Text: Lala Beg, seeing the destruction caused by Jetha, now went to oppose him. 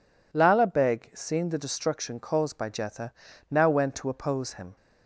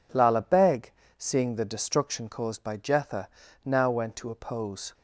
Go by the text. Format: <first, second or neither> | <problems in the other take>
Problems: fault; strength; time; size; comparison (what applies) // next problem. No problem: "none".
first | stops before "him"; at 4.9 s